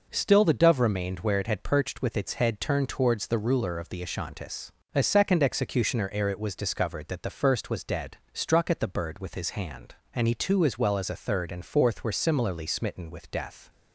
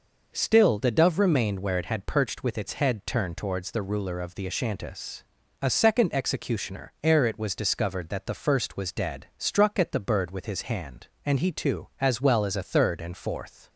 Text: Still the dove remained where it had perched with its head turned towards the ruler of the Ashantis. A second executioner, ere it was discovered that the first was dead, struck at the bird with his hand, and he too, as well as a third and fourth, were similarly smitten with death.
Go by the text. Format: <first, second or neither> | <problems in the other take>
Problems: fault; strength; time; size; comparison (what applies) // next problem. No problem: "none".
first | stops before "were similarly smitten with death"; at 13.6 s